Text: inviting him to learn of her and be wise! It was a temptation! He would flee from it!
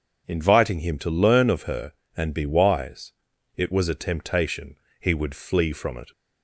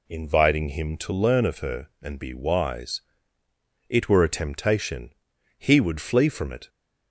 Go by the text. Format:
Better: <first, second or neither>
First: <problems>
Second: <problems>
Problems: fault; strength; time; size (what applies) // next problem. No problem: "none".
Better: first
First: none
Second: says "were" for "was"; at 4.0 s